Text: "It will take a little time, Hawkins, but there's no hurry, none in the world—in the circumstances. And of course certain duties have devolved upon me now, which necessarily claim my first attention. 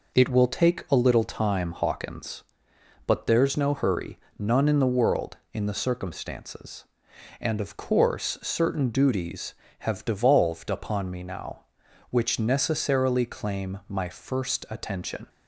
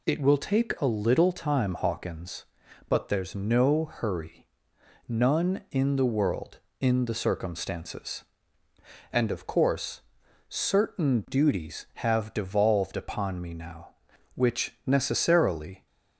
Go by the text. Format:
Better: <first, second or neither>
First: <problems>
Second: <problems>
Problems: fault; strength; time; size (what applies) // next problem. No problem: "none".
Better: first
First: none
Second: pauses between "course" and "certain"; noticeable; at 10.0 s; 0.48 s long // stops before "claim my first attention"; at 15.8 s